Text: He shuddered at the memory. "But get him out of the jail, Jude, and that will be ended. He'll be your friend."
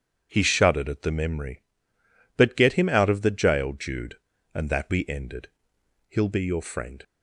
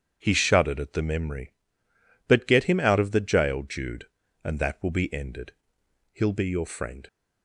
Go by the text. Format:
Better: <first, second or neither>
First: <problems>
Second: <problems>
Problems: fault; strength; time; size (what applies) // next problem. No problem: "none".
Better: second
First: starts louder than the rest; strong; until 1.3 s; 8 dB // skips "will"; at 4.9 s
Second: starts louder than the rest; strong; until 1.2 s; 8 dB